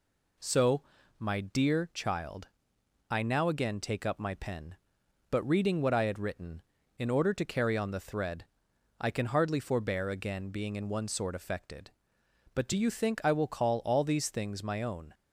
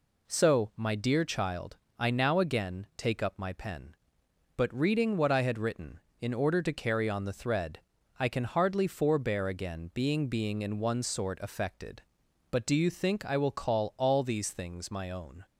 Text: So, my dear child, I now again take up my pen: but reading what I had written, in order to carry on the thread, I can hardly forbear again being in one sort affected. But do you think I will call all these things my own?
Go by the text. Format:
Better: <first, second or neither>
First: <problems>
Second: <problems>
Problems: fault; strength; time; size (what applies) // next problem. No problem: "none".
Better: first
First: none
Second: says "being" twice; at 10.2 s